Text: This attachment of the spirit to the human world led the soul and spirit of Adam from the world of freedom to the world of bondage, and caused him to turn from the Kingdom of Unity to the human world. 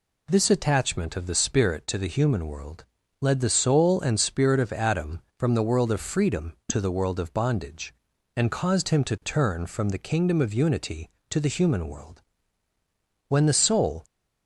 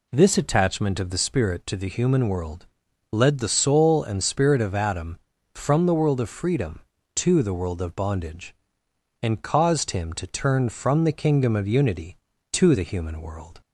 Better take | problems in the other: second | pauses between "world" and "led"; at 2.8 s; 0.38 s long; noticeable in the second // goes on to say "When the soul"; noticeable; from 13.2 s on; 0.76 s long

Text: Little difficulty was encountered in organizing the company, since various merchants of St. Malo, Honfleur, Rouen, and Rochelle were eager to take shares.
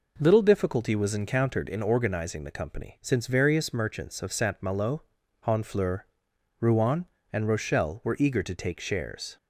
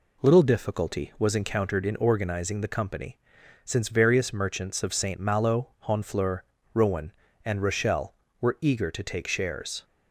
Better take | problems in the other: neither | none

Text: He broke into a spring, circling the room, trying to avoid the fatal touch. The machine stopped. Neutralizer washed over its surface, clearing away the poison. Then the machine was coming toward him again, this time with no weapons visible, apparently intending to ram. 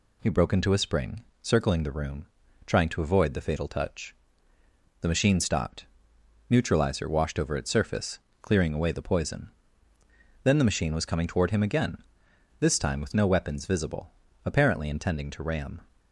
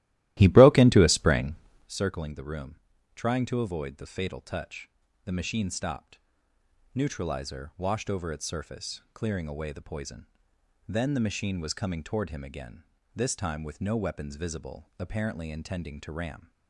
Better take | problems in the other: first | starts louder than the rest; strong; until 1.9 s; 16 dB

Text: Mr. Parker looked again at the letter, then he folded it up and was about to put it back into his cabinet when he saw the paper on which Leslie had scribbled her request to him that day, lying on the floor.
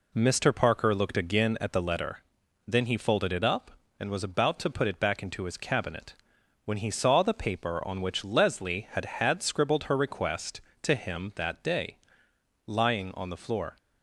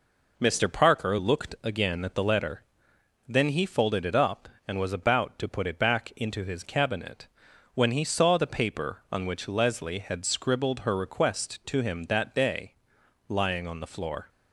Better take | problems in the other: second | pauses between "cabinet" and "when"; noticeable; at 6.1 s; 0.52 s long; noticeable in the second // says "had" twice; at 9.0 s

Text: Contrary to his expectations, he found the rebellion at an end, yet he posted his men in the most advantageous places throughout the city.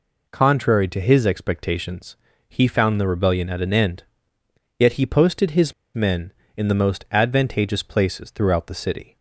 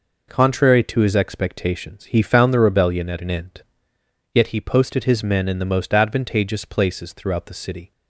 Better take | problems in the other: second | pauses between "his" and "men"; slight; at 5.7 s; 0.22 s long

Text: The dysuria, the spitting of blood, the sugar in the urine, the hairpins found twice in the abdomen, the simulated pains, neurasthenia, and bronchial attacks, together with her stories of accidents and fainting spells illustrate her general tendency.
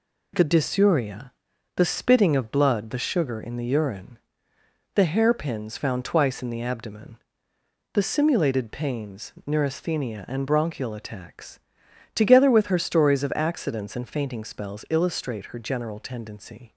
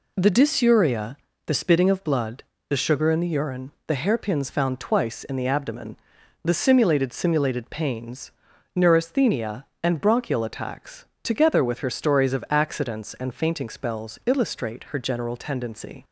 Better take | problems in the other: first | says "simulated" twice; at 7.1 s

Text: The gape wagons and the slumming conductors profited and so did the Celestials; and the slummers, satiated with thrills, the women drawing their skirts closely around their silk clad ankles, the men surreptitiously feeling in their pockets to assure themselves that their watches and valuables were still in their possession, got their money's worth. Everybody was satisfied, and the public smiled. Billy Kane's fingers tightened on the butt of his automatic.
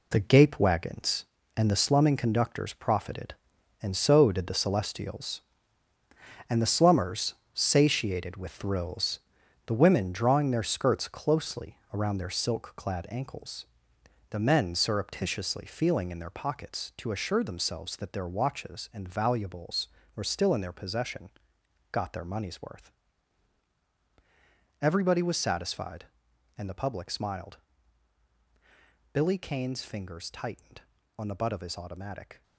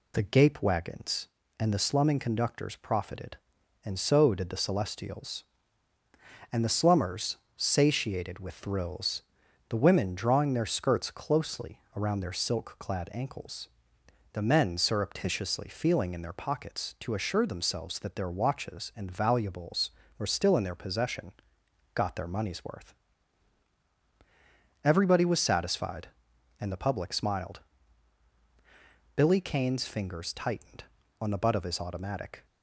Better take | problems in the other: second | gets quieter; strong; throughout; 9.5 dB // pauses between "closely" and "around"; slight; at 11.7 s; 0.16 s long; slight in the second

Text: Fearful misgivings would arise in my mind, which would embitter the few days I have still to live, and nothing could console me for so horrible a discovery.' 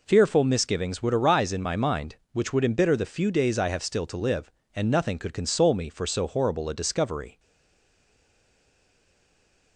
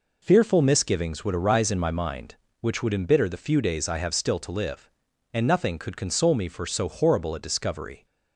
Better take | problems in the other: second | stays silent after the last word; from 7.3 s on; 2.4 s long

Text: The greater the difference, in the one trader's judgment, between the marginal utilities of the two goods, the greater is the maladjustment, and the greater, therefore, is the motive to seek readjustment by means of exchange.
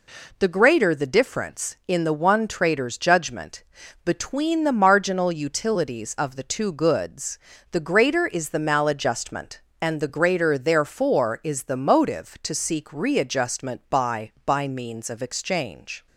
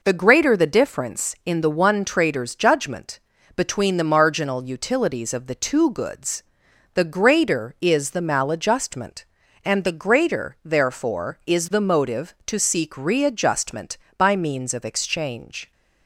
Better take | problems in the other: second | says "by" twice; at 14.4 s

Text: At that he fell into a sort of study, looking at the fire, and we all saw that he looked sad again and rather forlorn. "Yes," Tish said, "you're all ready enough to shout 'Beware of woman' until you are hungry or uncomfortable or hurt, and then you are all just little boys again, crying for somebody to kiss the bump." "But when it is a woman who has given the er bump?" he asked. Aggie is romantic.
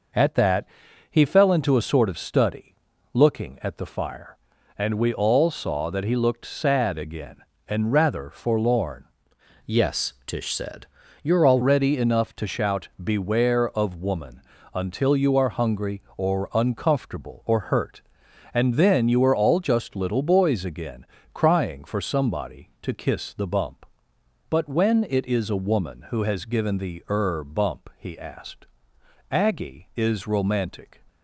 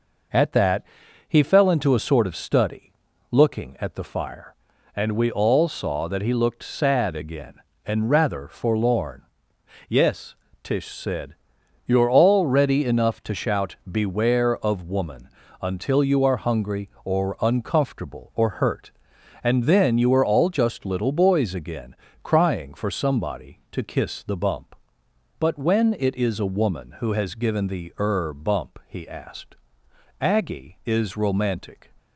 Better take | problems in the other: second | pauses between "that" and "he"; at 0.6 s; 0.44 s long; also in the second // changes voice from "Yes" to "all"; from 9.6 to 11.6 s; 2.0 s long // pauses between "woman" and "until"; slight; at 14.4 s; 0.34 s long; slight in the second

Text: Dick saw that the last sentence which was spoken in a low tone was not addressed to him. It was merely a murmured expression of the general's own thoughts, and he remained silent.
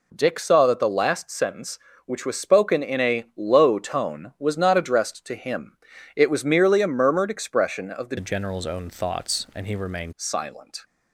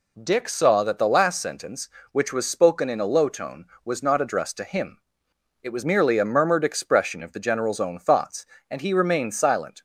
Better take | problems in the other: second | changes voice from "general's" to "remained"; from 8.1 to 10.1 s; 2.0 s long

